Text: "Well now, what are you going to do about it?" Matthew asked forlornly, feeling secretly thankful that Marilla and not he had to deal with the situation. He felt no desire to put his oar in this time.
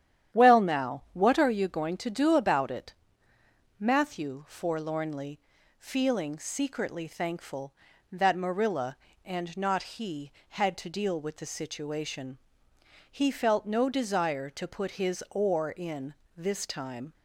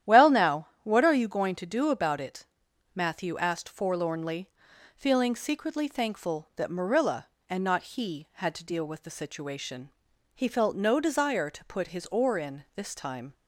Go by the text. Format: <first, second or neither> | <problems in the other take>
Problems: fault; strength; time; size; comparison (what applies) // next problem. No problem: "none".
second | starts louder than the rest; strong; until 1.4 s; 10.5 dB; strong in the second // skips "asked"; at 4.4 s // pauses between "in" and "this"; slight; at 16.1 s; 0.22 s long